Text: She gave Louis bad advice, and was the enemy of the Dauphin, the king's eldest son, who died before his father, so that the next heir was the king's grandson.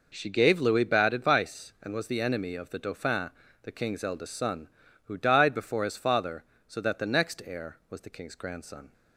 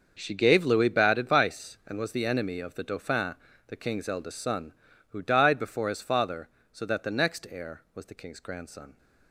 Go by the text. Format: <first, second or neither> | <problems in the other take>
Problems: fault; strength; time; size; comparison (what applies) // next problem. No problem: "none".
first | gets quieter; strong; throughout; 14 dB